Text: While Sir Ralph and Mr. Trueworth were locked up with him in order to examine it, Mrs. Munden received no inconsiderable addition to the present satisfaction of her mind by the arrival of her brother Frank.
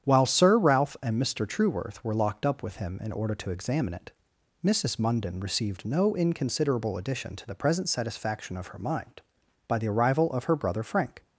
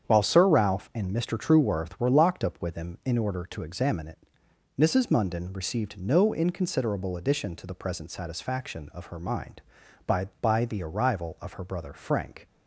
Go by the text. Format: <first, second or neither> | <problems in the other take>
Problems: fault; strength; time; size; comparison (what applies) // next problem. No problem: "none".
first | starts louder than the rest; strong; until 1.0 s; 8 dB; strong in the first // says "by" twice; at 10.4 s